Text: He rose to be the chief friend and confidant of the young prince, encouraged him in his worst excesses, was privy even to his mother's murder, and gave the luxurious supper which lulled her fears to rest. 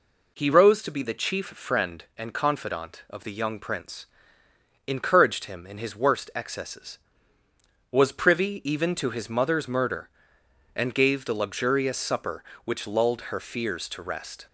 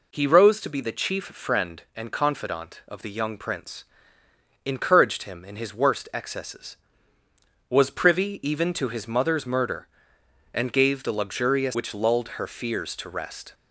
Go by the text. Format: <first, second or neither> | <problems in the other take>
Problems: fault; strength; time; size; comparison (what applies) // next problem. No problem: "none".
first | skips "supper"; at 11.7 s